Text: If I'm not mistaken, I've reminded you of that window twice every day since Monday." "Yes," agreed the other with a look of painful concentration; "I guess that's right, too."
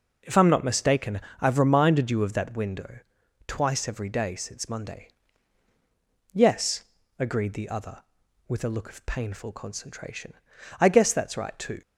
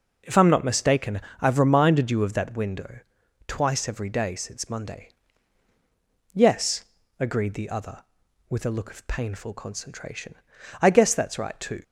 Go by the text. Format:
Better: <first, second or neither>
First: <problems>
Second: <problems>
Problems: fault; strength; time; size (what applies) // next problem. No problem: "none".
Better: neither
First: pauses between "window" and "twice"; noticeable; at 2.9 s; 0.48 s long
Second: pauses between "window" and "twice"; noticeable; at 2.9 s; 0.48 s long